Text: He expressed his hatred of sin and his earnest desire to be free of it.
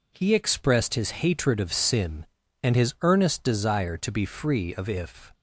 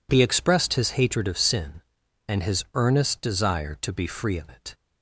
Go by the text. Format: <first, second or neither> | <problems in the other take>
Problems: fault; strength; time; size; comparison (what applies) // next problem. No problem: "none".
second | says "if" for "it"; at 4.8 s